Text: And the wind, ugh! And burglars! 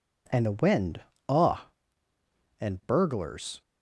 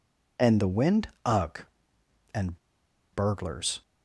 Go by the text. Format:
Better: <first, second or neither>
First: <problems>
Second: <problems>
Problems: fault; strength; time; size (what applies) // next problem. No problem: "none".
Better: first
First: none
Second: pauses between "And" and "burglars"; noticeable; at 2.5 s; 0.55 s long